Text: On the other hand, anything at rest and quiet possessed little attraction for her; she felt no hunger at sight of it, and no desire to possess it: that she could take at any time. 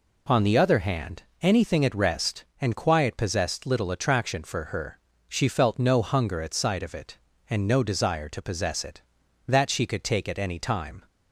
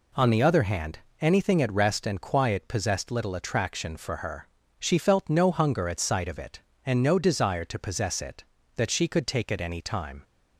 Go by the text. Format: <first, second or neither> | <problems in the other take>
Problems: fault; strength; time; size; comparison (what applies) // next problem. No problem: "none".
neither | none